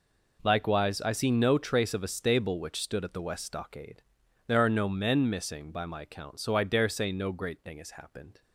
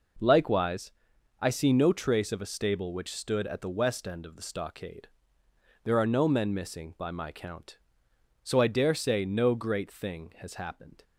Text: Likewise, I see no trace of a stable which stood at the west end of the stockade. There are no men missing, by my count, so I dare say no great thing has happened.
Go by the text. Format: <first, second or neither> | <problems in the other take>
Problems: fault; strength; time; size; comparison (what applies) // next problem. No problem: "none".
second | skips "end of the"; at 3.4 s